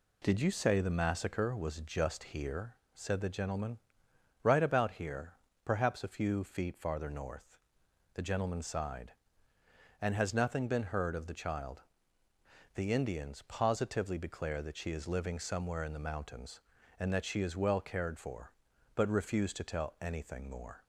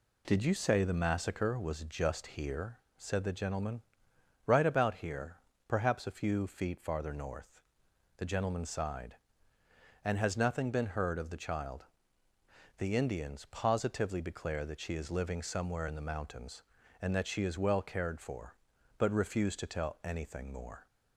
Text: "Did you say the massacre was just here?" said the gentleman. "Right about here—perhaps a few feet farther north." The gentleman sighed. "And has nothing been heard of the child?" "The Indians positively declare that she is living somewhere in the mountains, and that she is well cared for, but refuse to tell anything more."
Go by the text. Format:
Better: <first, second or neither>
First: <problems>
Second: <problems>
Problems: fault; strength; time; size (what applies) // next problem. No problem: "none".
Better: neither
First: none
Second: none